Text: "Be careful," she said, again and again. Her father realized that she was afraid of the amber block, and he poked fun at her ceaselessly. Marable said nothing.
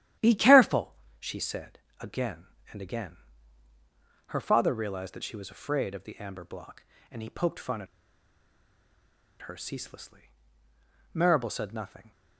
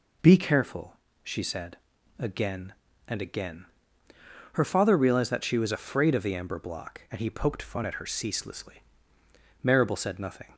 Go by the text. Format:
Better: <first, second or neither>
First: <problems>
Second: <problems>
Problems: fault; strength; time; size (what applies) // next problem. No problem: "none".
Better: second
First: starts louder than the rest; strong; until 1.4 s; 11.5 dB // pauses between "at" and "her"; strong; at 7.8 s; 1.5 s long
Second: none